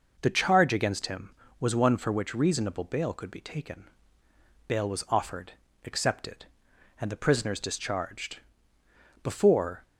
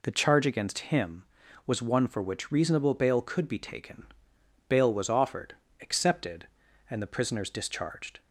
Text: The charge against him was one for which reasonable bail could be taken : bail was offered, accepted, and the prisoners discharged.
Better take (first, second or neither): second